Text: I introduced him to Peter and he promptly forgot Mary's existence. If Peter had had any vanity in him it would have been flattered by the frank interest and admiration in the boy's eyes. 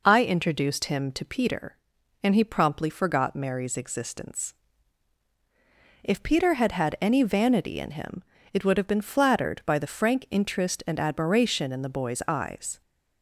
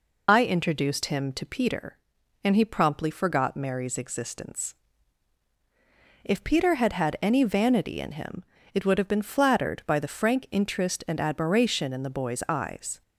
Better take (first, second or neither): first